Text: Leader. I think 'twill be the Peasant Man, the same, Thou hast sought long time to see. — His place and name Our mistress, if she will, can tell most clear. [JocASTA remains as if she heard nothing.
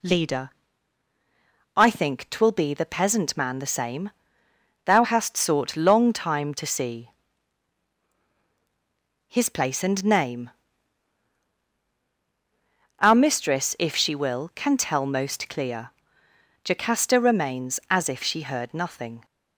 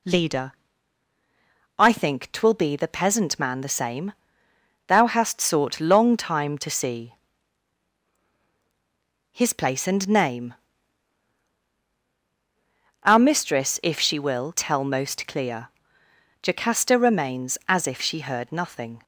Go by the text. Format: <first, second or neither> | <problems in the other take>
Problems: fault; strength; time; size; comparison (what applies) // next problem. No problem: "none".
first | pauses between "name" and "Our"; strong; at 10.5 s; 2.4 s long; strong in the first // skips "can"; at 14.5 s